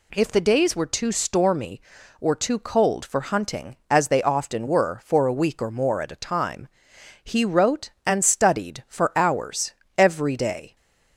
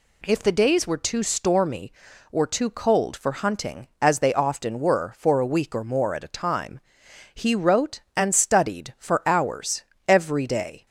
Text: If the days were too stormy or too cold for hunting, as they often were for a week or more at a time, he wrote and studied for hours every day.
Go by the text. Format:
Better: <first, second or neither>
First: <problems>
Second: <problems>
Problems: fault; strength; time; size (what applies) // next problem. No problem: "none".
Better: neither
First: pauses between "hours" and "every"; slight; at 9.7 s; 0.24 s long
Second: pauses between "hours" and "every"; slight; at 9.8 s; 0.24 s long